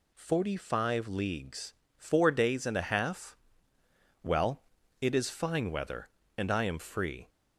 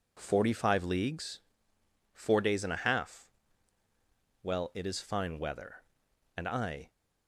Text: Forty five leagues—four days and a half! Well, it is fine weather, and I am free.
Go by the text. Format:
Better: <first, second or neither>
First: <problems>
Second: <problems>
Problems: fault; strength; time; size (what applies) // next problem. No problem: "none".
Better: first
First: none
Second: stops before "am free"; at 6.8 s